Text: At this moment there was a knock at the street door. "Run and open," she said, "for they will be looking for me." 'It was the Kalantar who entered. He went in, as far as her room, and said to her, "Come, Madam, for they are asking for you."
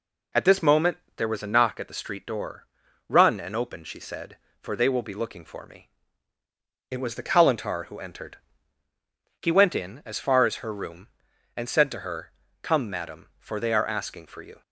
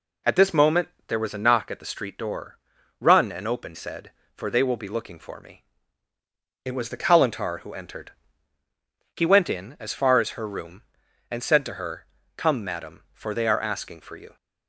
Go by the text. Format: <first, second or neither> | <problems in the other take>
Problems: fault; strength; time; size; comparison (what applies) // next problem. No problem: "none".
first | pauses between "moment" and "there"; slight; at 0.8 s; 0.20 s long; slight in the first // skips "she"; at 3.7 s